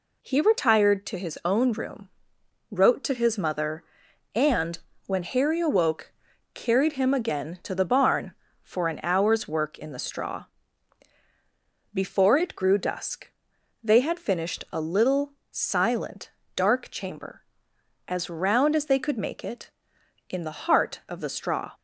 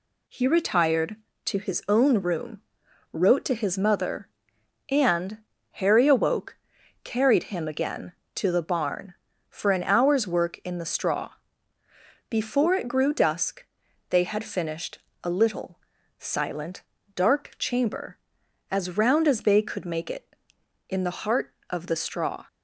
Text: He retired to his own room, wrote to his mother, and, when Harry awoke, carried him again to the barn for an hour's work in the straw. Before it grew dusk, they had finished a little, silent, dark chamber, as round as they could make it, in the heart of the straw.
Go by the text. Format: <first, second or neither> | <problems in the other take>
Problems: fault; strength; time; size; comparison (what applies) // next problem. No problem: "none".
first | skips "when"; at 5.5 s // pauses between "finished" and "a"; slight; at 14.9 s; 0.24 s long